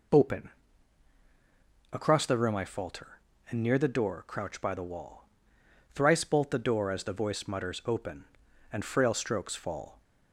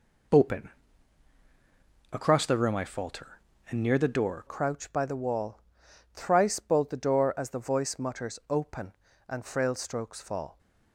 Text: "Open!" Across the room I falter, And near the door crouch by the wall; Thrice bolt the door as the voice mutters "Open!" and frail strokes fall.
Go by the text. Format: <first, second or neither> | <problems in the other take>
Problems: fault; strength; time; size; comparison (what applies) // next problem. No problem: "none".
first | changes voice at "crouch"; from 4.4 s on; 6.1 s long